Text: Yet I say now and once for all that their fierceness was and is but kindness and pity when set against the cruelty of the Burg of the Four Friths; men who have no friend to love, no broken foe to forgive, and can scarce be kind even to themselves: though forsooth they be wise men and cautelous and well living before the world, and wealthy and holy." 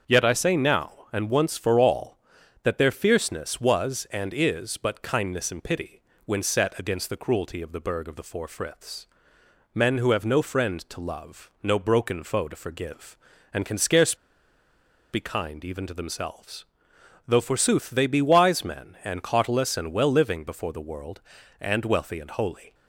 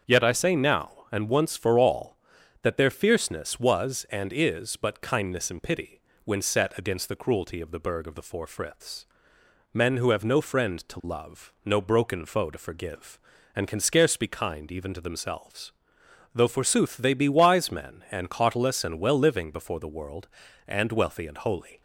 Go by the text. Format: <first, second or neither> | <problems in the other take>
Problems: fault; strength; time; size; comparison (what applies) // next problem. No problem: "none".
second | starts louder than the rest; strong; until 1.2 s; 7.5 dB; strong in the second // pauses between "pity" and "when"; slight; at 6.0 s; 0.24 s long; slight in the second // pauses between "scarce" and "be"; noticeable; at 14.1 s; 0.97 s long